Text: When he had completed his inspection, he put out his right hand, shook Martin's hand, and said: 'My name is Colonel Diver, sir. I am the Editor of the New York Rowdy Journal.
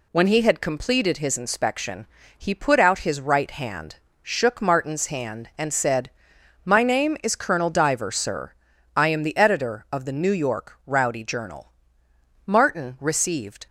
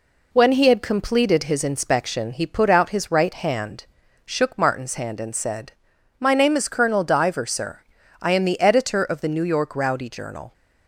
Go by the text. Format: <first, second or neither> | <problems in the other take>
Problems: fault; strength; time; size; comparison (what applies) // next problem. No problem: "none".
second | goes on to say "Martin received"; noticeable; from 12.4 s on; 1.2 s long